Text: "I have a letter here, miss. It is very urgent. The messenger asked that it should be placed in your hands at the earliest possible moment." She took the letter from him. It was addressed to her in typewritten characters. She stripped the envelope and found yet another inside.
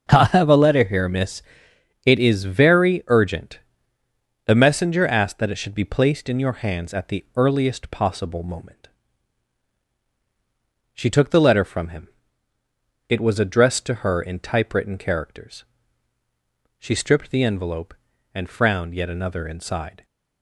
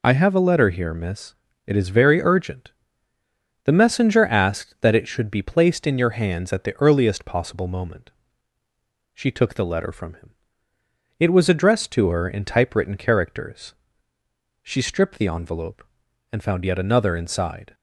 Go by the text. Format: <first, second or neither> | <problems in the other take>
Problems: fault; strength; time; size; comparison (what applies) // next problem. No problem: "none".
second | starts louder than the rest; until 1.1 s; 7 dB // says "frowned" for "found"; at 18.4 s